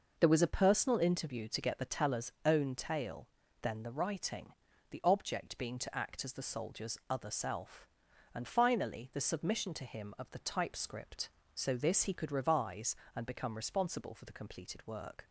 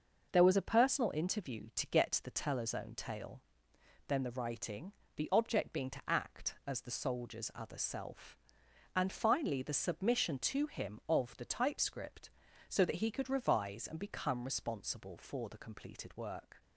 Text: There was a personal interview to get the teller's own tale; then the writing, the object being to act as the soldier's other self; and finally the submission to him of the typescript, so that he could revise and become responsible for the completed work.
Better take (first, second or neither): second